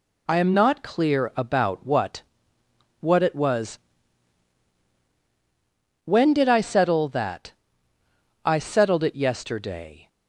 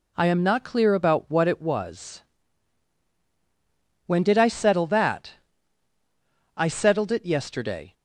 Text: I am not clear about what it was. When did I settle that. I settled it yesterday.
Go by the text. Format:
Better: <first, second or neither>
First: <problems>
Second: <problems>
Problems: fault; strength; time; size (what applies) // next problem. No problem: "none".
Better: second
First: says "what" twice; at 2.9 s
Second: none